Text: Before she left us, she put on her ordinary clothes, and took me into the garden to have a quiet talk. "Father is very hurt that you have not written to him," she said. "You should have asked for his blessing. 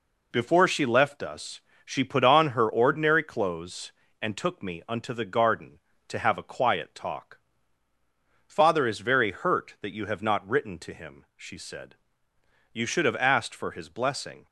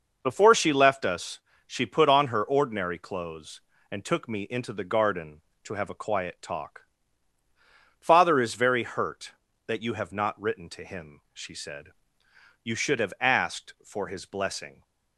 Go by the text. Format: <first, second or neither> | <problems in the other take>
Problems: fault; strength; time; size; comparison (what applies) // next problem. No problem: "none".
second | says "unto" for "into"; at 4.8 s